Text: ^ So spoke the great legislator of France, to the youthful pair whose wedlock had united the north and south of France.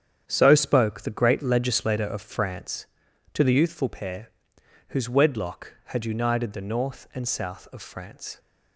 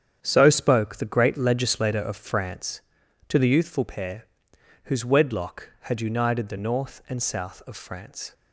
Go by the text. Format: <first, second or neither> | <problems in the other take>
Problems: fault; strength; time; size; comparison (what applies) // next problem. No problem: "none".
neither | starts louder than the rest; strong; the same in both // pauses between "pair" and "whose"; noticeable; the same in both